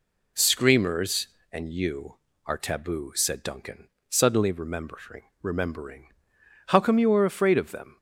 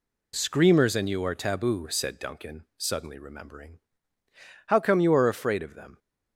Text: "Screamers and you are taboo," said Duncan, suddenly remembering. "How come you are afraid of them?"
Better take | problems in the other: second | says "remembering" twice; at 5.4 s

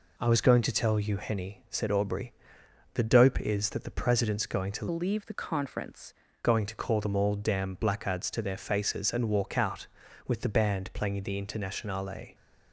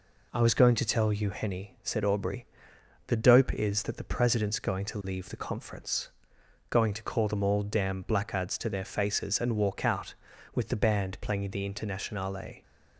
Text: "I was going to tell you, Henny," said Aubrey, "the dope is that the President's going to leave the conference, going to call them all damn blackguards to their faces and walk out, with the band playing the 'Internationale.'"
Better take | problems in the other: second | changes voice from "leave" to "conference"; from 4.9 to 6.1 s; 1.2 s long

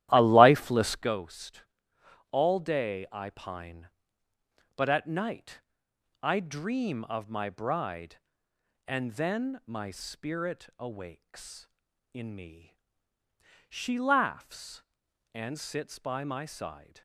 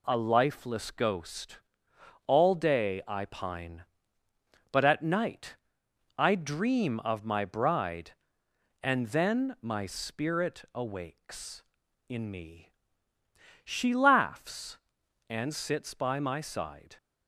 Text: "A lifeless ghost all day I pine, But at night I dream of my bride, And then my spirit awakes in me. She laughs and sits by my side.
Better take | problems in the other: second | starts louder than the rest; strong; until 1.1 s; 13 dB // pauses between "ghost" and "all"; noticeable; at 1.6 s; 0.66 s long; noticeable in the second // pauses between "night" and "I"; noticeable; at 5.6 s; 0.62 s long; noticeable in the second

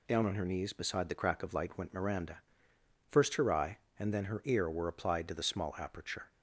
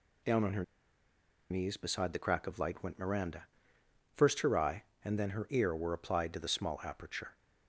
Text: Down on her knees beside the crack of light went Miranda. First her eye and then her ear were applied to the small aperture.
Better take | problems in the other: first | pauses between "her" and "knees"; noticeable; at 0.6 s; 0.87 s long

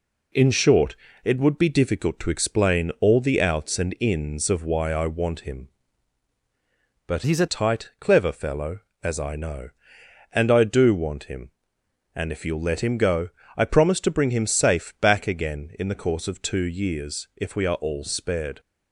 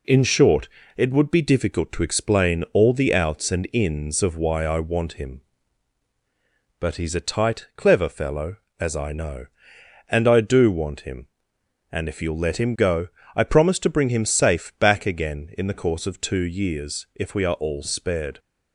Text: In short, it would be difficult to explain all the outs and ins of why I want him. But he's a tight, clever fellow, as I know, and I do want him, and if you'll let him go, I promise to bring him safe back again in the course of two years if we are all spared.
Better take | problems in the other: second | changes voice from "he's" to "a"; from 7.2 to 7.4 s; 0.2 s long

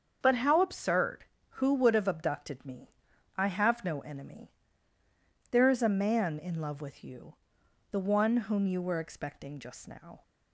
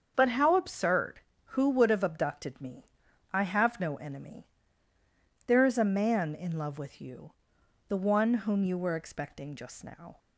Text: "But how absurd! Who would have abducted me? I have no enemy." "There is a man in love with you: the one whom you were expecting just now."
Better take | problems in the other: neither | starts louder than the rest; the same in both

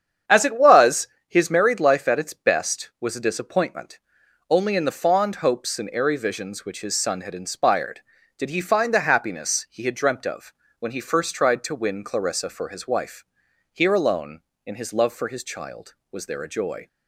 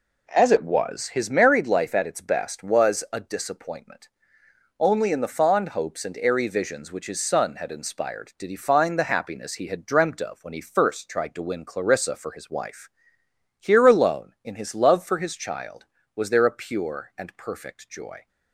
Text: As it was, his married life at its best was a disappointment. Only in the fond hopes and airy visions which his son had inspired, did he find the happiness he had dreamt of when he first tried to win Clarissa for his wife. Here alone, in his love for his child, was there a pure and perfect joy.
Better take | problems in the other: second | starts louder than the rest; strong; until 1.4 s; 8 dB // pauses between "of" and "when"; slight; at 10.5 s; 0.26 s long // skips "pure and perfect"; at 16.4 s

